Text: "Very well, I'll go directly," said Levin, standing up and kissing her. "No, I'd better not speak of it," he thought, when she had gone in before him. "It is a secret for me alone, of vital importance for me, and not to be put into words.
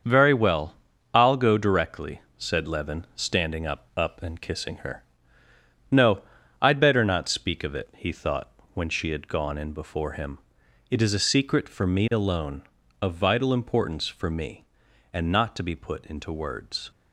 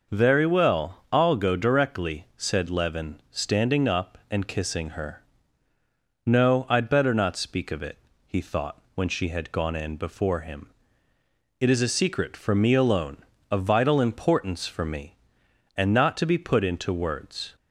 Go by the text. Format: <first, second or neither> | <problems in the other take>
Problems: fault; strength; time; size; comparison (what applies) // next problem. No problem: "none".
second | starts louder than the rest; until 1.4 s; 7 dB // says "up" twice; at 3.9 s